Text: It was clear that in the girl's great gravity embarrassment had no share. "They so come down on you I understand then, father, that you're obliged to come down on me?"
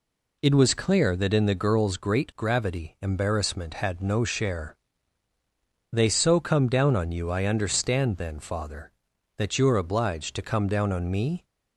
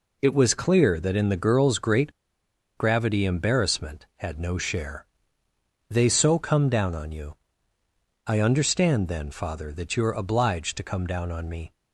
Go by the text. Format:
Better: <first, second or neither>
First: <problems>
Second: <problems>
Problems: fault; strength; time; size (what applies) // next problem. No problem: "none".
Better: first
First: none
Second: pauses between "great" and "gravity"; noticeable; at 2.1 s; 0.65 s long // pauses between "you" and "I"; noticeable; at 7.3 s; 0.90 s long